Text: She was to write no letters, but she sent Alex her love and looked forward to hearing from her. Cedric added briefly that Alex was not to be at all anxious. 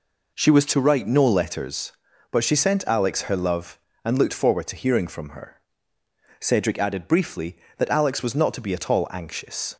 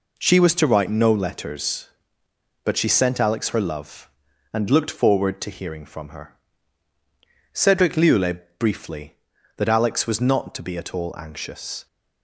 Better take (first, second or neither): first